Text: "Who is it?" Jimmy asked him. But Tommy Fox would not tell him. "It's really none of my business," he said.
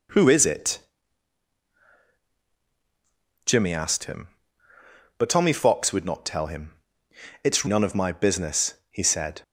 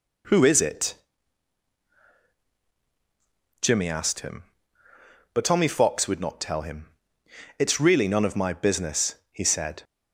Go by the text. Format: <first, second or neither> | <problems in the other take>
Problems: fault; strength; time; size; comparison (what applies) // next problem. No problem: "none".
second | skips "really"; at 7.6 s